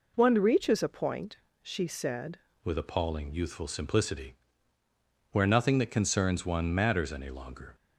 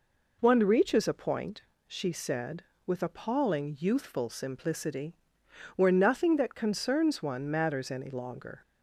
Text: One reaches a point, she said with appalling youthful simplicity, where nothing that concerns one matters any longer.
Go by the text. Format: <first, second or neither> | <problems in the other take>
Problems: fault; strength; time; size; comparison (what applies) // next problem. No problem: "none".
second | changes voice at "with"; from 2.6 s on; 5.1 s long